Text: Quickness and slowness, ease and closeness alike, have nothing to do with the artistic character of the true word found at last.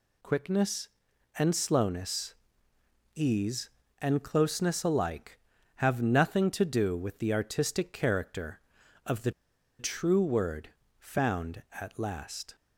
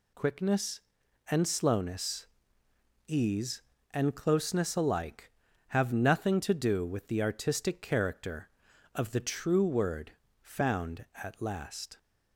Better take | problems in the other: second | pauses between "the" and "true"; noticeable; at 9.3 s; 0.48 s long // pauses between "word" and "found"; slight; at 10.6 s; 0.30 s long; slight in the second

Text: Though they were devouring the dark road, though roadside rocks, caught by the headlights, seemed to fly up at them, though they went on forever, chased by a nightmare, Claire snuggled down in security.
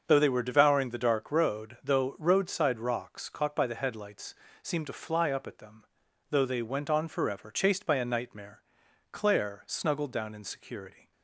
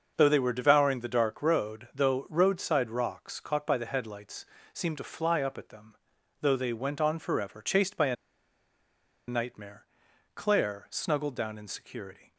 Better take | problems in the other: first | starts louder than the rest; noticeable; until 1.1 s; 6 dB; also in the first // pauses between "a" and "nightmare"; at 8.1 s; 1.1 s long

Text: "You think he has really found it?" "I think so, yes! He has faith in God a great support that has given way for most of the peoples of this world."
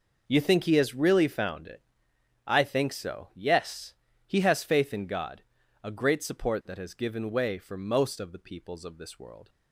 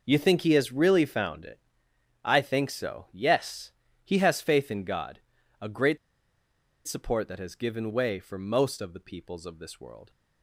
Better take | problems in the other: first | pauses between "God" and "a"; at 5.2 s; 0.40 s long; also in the first // pauses between "great" and "support"; noticeable; at 5.9 s; 0.90 s long

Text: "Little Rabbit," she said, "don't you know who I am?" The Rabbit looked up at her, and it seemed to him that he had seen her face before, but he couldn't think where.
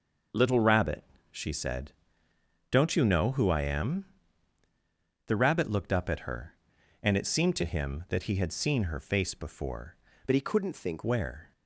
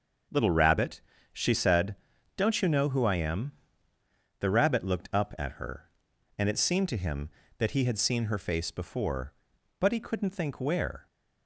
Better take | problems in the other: second | starts louder than the rest; until 1.6 s; 6 dB; also in the second // changes voice from "but" to "think"; from 10.2 to 11.0 s; 0.8 s long

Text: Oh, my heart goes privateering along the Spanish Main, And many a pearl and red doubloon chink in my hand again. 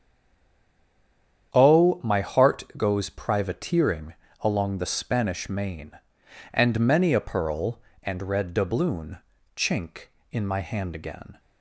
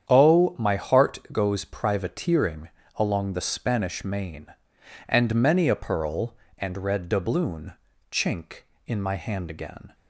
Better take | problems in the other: second | stays silent before the first word; noticeable; until 1.5 s; 1.5 s long // starts louder than the rest; strong; until 2.5 s; 9 dB; strong in the second // pauses between "privateering" and "along"; slight; at 4.1 s; 0.28 s long; slight in the second // pauses between "doubloon" and "chink"; at 9.1 s; 0.38 s long; also in the second

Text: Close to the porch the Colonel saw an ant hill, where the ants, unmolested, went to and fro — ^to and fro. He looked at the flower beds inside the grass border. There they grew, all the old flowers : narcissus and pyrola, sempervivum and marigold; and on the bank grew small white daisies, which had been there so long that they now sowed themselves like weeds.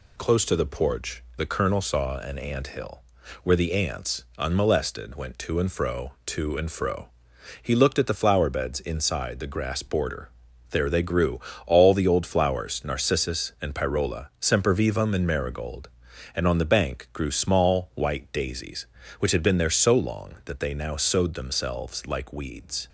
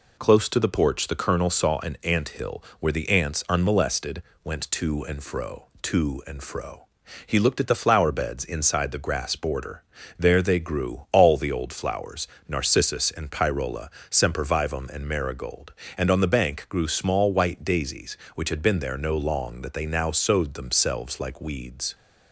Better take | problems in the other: first | says "no" for "so"; at 18.9 s

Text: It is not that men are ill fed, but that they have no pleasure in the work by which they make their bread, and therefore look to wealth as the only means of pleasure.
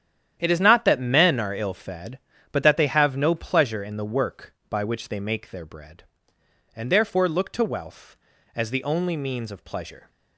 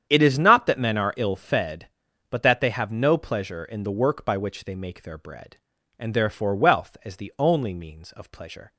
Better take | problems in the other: first | starts louder than the rest; strong; until 1.1 s; 9 dB; strong in the first // skips "look to"; at 6.5 s

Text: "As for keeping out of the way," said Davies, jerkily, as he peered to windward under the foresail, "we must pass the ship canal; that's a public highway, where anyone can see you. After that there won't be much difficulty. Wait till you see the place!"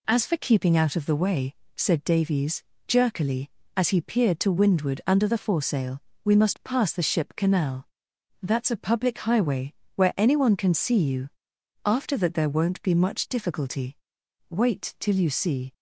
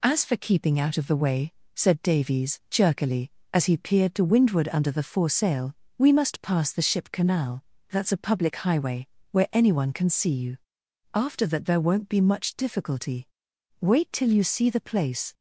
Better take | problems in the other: second | stops before "the place"; at 15.7 s

